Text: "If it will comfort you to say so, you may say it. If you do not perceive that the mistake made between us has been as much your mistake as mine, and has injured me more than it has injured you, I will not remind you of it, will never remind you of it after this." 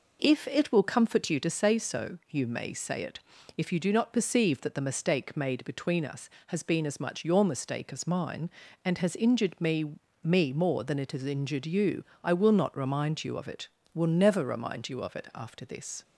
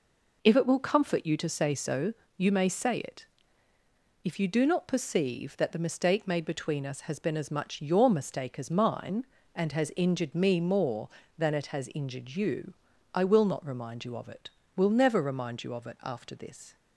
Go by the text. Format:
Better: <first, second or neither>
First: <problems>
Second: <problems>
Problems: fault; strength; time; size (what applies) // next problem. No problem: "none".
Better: second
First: says "me" twice; at 10.2 s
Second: none